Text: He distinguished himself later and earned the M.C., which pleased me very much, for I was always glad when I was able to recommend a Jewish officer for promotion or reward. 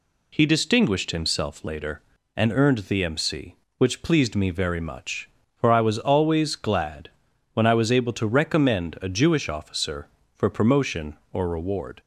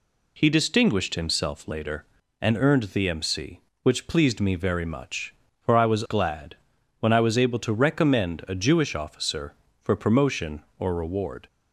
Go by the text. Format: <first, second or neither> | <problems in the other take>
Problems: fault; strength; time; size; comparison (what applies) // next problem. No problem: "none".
first | skips "always"; at 6.0 s // pauses between "glad" and "when"; at 6.5 s; 0.42 s long; also in the first